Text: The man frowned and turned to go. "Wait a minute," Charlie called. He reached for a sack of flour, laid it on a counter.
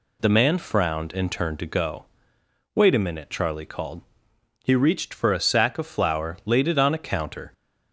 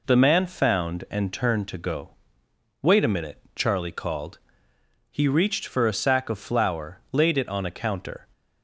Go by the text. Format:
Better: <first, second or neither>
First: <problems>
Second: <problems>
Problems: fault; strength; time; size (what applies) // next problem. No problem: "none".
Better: first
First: none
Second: says "found" for "frowned"; at 0.4 s